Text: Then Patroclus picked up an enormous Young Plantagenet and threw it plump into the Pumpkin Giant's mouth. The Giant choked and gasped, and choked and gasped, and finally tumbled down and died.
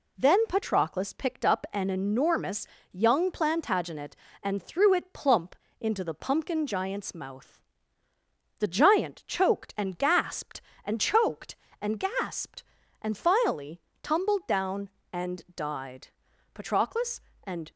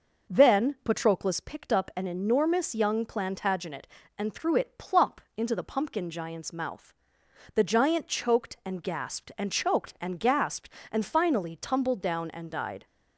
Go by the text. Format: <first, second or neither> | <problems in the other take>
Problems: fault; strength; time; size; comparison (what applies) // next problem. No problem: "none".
second | pauses between "enormous" and "Young"; slight; at 2.6 s; 0.26 s long // pauses between "plump" and "into"; slight; at 5.5 s; 0.24 s long; slight in the second // pauses between "finally" and "tumbled"; slight; at 13.7 s; 0.24 s long // goes on to say "Patroclus and"; noticeable; from 16.5 s on; 1.1 s long